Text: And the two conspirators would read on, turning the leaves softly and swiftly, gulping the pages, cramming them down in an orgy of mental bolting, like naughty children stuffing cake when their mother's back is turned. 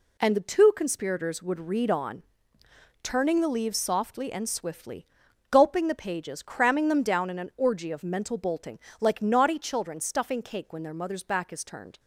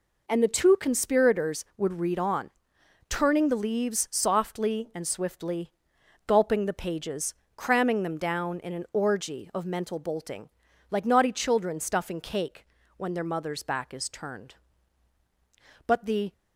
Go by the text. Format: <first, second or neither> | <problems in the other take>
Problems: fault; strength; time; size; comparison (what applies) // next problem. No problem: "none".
first | pauses between "cake" and "when"; slight; at 12.6 s; 0.30 s long // goes on to say "But the"; slight; from 15.8 s on; 0.46 s long